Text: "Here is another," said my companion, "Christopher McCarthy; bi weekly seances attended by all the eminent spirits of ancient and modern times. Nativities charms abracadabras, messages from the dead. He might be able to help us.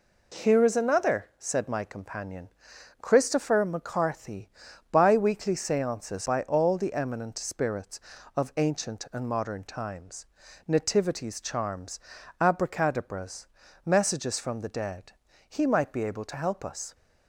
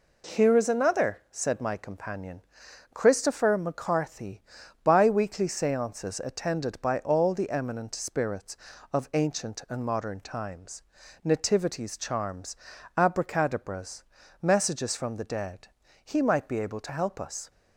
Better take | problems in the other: second | skips "attended"; at 6.2 s // pauses between "charms" and "abracadabras"; at 11.9 s; 0.42 s long; also in the second

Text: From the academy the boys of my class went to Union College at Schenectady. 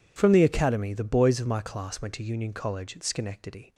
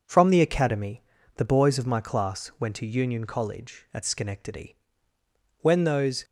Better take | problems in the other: first | pauses between "academy" and "the"; slight; at 1.0 s; 0.35 s long // goes on to say "When those"; noticeable; from 5.6 s on; 0.64 s long

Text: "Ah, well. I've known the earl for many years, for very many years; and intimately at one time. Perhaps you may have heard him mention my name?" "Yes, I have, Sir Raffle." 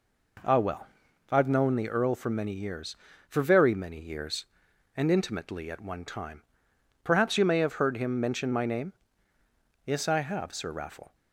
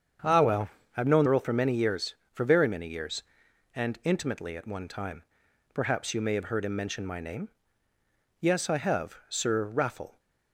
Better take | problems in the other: first | starts louder than the rest; strong; until 1.5 s; 7.5 dB // skips "the"; at 1.2 s

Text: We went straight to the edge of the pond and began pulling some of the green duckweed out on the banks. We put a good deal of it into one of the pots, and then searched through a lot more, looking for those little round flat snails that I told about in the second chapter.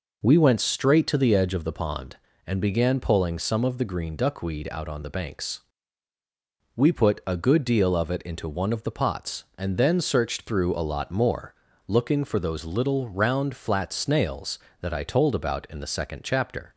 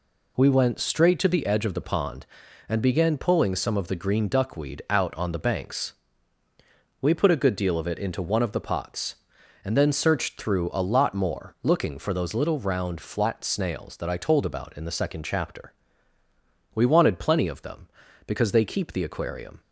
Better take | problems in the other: first | goes on to say "We wanted plenty of them because they keep the aquarium"; strong; from 16.7 s on; 2.8 s long

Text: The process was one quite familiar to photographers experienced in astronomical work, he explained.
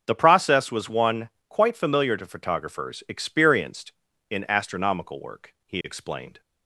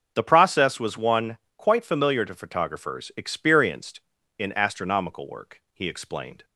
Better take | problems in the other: neither | starts louder than the rest; the same in both // pauses between "one" and "quite"; slight; the same in both

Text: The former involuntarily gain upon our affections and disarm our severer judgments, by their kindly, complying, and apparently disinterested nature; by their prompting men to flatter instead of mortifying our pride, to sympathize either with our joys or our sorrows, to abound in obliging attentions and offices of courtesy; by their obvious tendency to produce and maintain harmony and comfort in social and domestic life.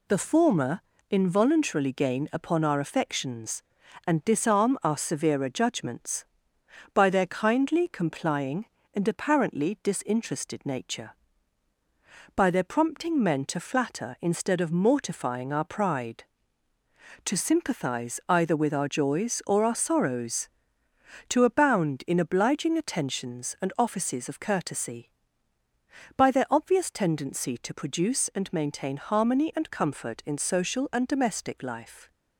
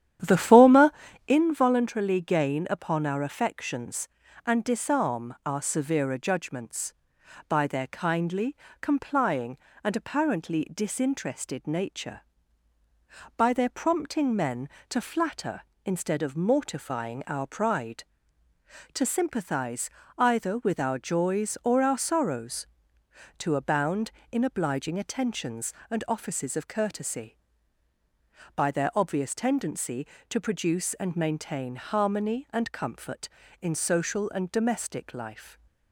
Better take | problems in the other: first | starts louder than the rest; strong; until 1.4 s; 10.5 dB // pauses between "former" and "involuntarily"; slight; at 0.9 s; 0.36 s long; slight in the first // pauses between "sympathize" and "either"; slight; at 19.8 s; 0.30 s long

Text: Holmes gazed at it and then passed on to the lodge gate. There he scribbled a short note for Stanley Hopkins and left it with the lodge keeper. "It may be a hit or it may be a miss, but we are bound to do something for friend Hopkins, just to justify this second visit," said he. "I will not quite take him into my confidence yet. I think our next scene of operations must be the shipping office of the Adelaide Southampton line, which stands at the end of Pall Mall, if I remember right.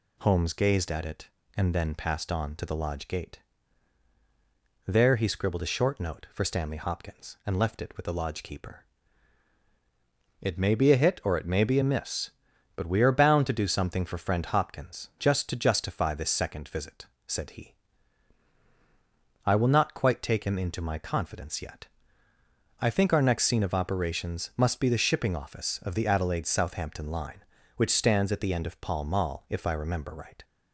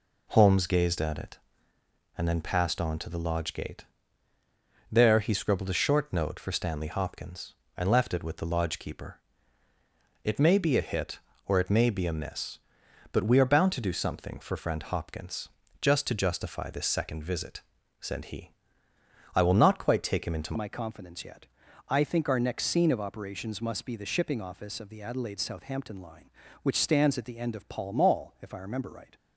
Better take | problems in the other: first | changes voice at "my"; from 20.5 s on; 8.6 s long

